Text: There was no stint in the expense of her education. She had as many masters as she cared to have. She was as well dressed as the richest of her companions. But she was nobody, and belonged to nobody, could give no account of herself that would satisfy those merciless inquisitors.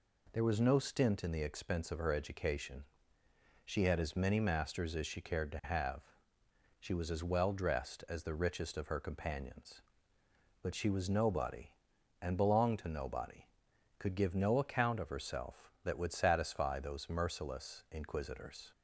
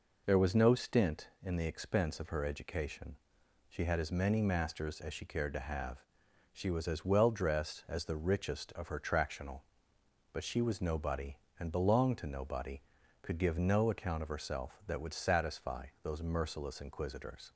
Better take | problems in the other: first | says "tractional" for "companions"; at 8.9 s // pauses between "satisfy" and "those"; slight; at 15.8 s; 0.16 s long

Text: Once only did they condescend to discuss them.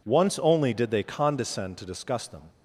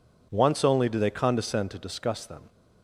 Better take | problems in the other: first | says "do" for "did"; at 0.8 s

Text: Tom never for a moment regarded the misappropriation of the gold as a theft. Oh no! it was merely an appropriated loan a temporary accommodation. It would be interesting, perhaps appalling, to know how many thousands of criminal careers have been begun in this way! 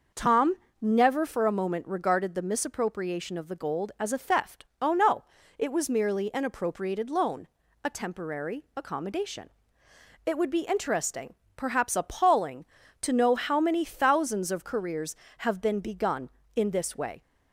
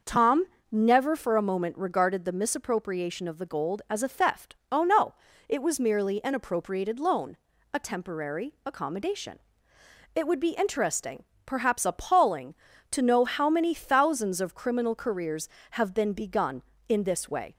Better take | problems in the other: second | pauses between "Tom" and "never"; slight; at 0.5 s; 0.26 s long; slight in the second // pauses between "loan" and "a"; slight; at 7.4 s; 0.36 s long; slight in the second // skips "criminal"; at 14.6 s

